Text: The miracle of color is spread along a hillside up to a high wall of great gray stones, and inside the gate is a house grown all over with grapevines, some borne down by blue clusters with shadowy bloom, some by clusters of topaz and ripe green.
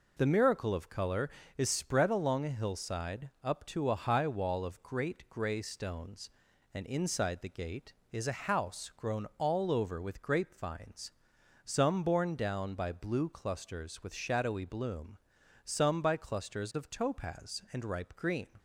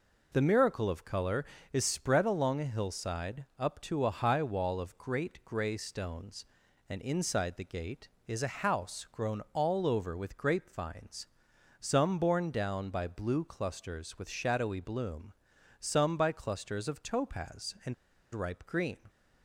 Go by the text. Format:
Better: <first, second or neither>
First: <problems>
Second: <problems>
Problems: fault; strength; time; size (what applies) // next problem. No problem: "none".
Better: first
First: none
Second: pauses between "and" and "ripe"; at 17.9 s; 0.37 s long